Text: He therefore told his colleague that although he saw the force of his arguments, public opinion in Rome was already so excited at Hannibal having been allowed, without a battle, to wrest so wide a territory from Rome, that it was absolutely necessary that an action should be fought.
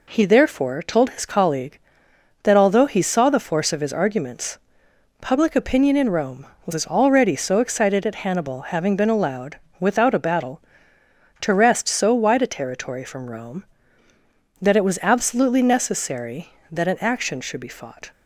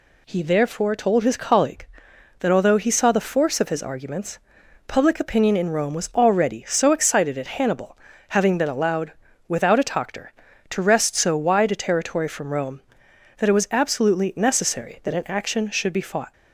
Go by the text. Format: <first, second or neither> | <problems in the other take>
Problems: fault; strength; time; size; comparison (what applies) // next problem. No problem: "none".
first | pauses between "Hannibal" and "having"; slight; at 7.9 s; 0.32 s long // says "toctor" for "battle"; at 9.8 s